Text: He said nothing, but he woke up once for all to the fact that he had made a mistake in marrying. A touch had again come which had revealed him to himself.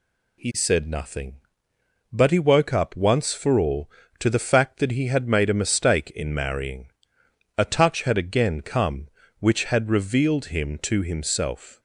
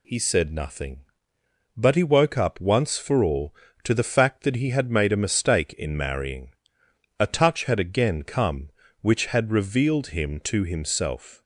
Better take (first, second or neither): neither